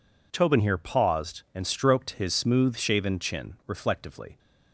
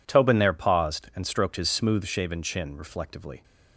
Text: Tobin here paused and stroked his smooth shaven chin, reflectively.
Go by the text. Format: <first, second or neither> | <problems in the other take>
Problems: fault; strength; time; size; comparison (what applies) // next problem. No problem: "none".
first | says "there" for "here"; at 0.3 s